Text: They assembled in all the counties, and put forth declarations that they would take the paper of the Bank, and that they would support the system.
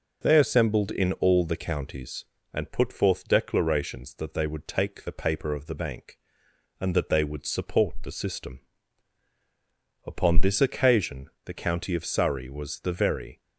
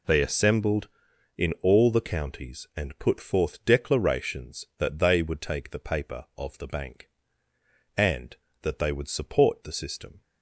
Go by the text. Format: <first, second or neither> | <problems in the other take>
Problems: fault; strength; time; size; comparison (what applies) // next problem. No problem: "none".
second | goes on to say "Upon this occasion the county of Surrey was the very"; strong; from 10.0 s on; 3.3 s long